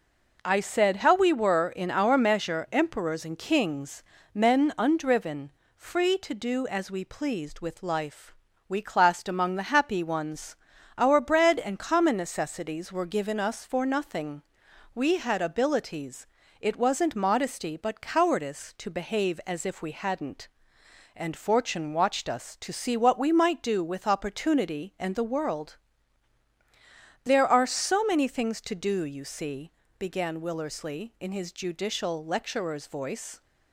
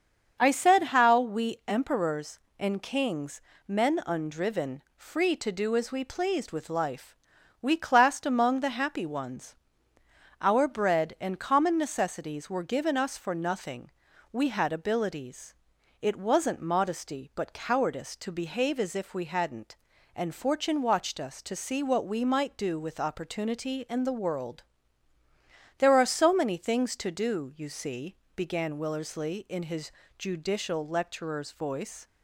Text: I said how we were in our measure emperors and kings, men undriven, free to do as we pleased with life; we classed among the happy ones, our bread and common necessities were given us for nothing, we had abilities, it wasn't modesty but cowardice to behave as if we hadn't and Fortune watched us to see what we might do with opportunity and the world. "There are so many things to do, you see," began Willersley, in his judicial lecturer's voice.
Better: first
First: none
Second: starts louder than the rest; until 1.4 s; 7 dB // skips "were in our measure"; at 1.6 s // pauses between "his" and "judicial"; slight; at 29.8 s; 0.28 s long

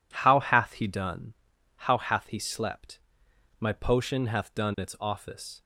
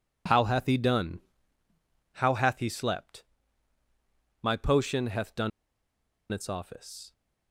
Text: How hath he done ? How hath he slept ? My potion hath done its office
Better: first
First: none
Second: pauses between "done" and "its"; noticeable; at 5.5 s; 0.82 s long

